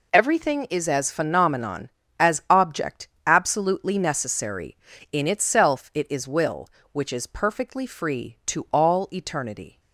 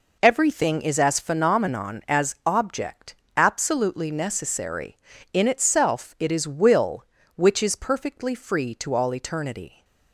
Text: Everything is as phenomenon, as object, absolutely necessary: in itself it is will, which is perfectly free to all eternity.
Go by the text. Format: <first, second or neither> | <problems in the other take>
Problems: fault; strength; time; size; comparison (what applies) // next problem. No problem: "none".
neither | none